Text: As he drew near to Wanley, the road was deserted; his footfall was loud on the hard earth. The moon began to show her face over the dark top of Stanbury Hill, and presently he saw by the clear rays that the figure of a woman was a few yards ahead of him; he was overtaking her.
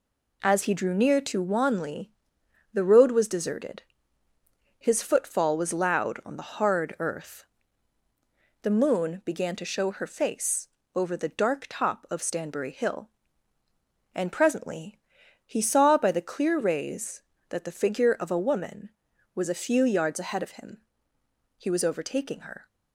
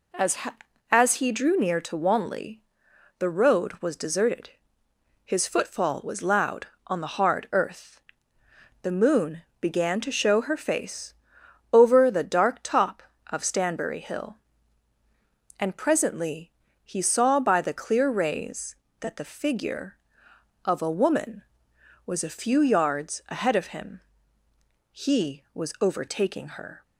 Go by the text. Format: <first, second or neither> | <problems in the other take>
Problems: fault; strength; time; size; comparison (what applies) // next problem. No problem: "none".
first | says "As" twice; at 0.8 s // pauses between "moon" and "began"; slight; at 9.4 s; 0.18 s long // pauses between "face" and "over"; noticeable; at 11.1 s; 0.60 s long; slight in the first // pauses between "presently" and "he"; slight; at 16.5 s; 0.34 s long; also in the first